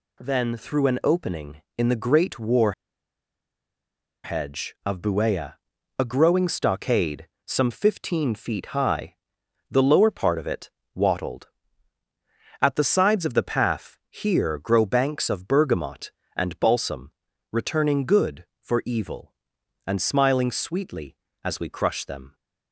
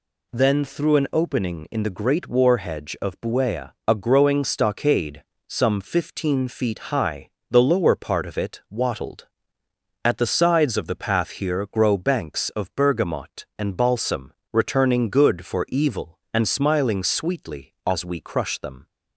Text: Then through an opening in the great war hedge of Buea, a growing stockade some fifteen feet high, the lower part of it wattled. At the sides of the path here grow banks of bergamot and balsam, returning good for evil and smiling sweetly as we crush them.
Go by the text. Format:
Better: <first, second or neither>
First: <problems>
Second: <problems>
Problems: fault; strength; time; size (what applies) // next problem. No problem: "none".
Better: second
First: pauses between "war" and "hedge"; strong; at 2.7 s; 1.5 s long // pauses between "stockade" and "some"; slight; at 7.2 s; 0.18 s long // pauses between "it" and "wattled"; slight; at 10.7 s; 0.24 s long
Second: pauses between "stockade" and "some"; slight; at 5.2 s; 0.26 s long